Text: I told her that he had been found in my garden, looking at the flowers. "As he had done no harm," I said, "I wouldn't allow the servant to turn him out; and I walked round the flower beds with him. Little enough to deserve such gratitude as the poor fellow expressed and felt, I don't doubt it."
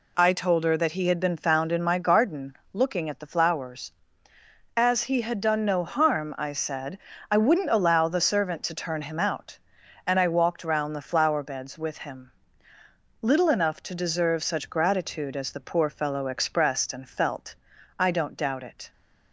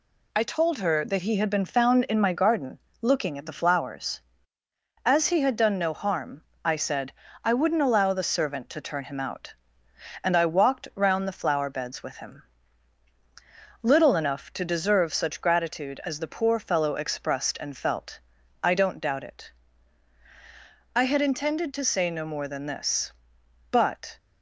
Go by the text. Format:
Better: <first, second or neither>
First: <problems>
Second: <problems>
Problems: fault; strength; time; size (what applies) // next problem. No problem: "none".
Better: first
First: none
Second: goes on to say "I had intended to say no more than this But"; strong; from 20.9 s on; 3.2 s long